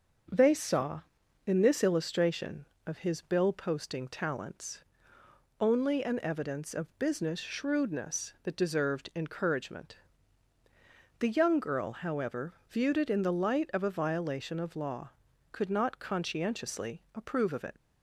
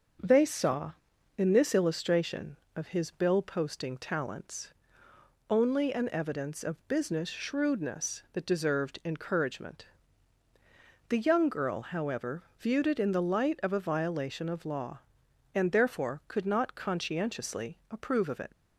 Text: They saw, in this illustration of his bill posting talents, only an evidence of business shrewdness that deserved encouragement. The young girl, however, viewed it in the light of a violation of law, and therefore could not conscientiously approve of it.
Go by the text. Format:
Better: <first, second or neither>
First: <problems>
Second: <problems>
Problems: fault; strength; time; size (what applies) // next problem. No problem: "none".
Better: second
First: starts louder than the rest; until 1.7 s; 6.5 dB // skips "and therefore"; at 15.3 s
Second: starts louder than the rest; until 1.6 s; 6.5 dB